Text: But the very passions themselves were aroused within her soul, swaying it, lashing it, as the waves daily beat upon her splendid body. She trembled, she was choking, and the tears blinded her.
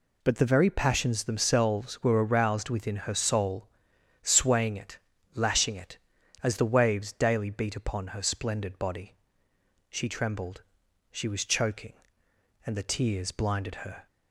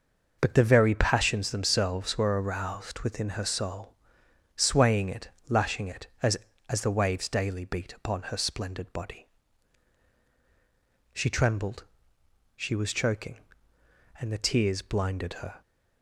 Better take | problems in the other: first | says "as" twice; at 6.7 s

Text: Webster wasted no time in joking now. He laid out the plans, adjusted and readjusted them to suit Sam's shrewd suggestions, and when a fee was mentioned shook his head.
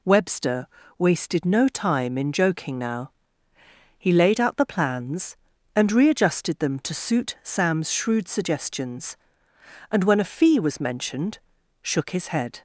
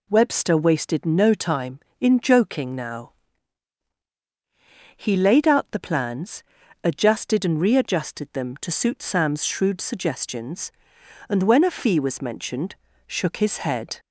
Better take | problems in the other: second | pauses between "Webster" and "wasted"; slight; at 0.6 s; 0.32 s long // skips "adjusted"; at 5.5 s // pauses between "mentioned" and "shook"; noticeable; at 11.3 s; 0.46 s long; slight in the second

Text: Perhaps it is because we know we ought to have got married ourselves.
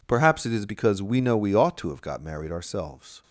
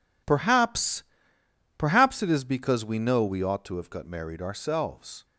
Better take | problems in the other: first | says "Perhaps" twice; at 1.7 s

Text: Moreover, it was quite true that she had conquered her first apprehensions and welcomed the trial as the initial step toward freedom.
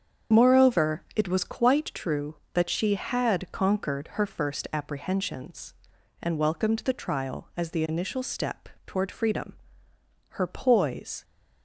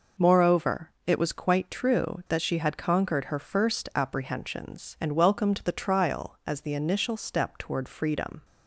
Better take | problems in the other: second | starts louder than the rest; strong; until 1.4 s; 7 dB // pauses between "step" and "toward"; slight; at 8.6 s; 0.20 s long // goes on to say "Her poise"; noticeable; from 10.2 s on; 0.94 s long

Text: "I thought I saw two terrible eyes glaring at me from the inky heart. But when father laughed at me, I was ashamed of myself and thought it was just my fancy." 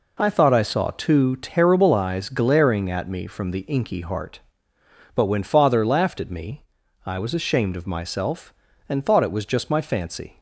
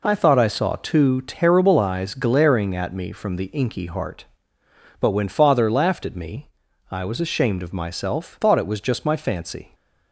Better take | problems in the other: first | skips "and"; at 8.4 s

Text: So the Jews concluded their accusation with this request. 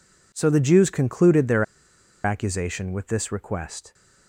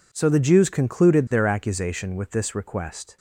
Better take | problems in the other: second | pauses between "their" and "accusation"; noticeable; at 1.6 s; 0.62 s long

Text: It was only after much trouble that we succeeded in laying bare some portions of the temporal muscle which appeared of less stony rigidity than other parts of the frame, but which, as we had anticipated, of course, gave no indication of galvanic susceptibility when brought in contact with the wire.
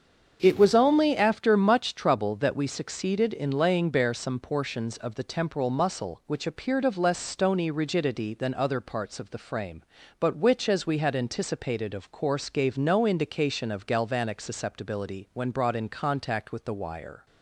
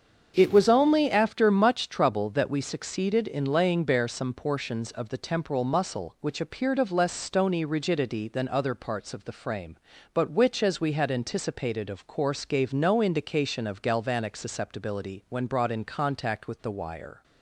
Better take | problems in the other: neither | starts louder than the rest; strong; the same in both

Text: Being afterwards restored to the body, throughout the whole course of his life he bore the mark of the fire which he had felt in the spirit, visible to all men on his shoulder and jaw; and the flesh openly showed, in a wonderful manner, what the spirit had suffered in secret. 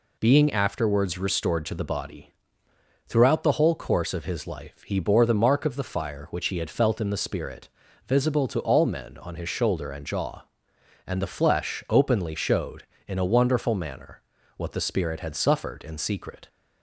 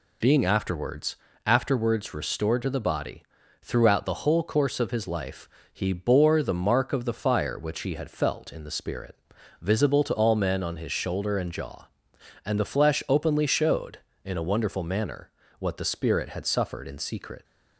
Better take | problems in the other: first | says "afterwards" twice; at 1.4 s // pauses between "life" and "he"; slight; at 5.4 s; 0.24 s long

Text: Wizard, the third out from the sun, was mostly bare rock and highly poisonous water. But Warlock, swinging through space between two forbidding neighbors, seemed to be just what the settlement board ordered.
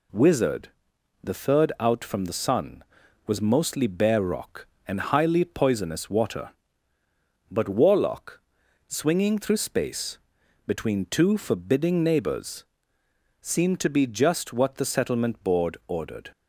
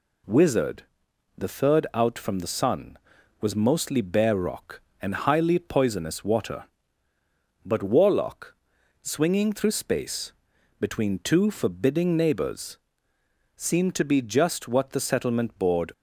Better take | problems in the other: first | pauses between "space" and "between"; noticeable; at 10.3 s; 0.47 s long; noticeable in the first // stops before "ordered"; at 15.9 s

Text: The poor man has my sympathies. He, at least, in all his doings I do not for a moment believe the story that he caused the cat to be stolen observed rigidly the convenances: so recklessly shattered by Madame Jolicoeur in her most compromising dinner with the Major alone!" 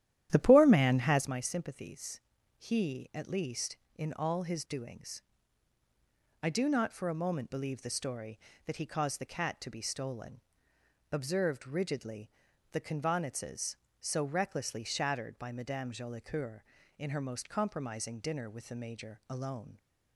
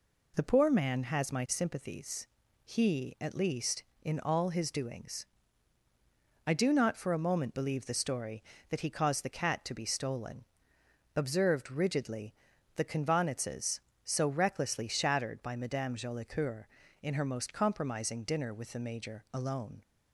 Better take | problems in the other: second | starts louder than the rest; strong; until 1.4 s; 12 dB // pauses between "doings" and "I"; at 5.2 s; 1.2 s long; also in the second // pauses between "stolen" and "observed"; noticeable; at 10.3 s; 0.72 s long; noticeable in the second // pauses between "rigidly" and "the"; at 12.3 s; 0.40 s long; also in the second

